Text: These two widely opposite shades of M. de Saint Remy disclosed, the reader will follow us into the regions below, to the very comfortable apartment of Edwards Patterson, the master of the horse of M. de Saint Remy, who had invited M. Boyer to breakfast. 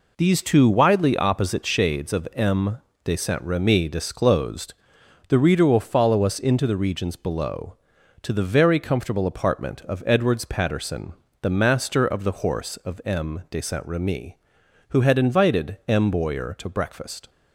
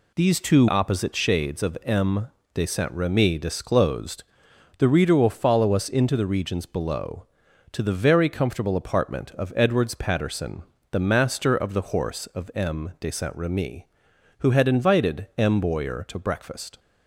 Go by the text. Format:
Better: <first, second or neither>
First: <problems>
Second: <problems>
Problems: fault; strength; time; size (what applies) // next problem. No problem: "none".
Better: first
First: none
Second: skips "widely"; at 0.6 s